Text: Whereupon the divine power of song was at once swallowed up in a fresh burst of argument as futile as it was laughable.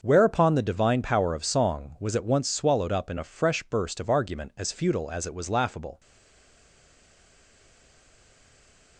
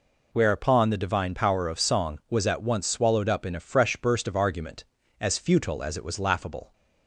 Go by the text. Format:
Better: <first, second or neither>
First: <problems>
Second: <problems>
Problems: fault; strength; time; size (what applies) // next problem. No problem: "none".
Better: second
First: starts louder than the rest; until 1.0 s; 6.5 dB // stays silent after the last word; strong; from 5.9 s on; 3.0 s long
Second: none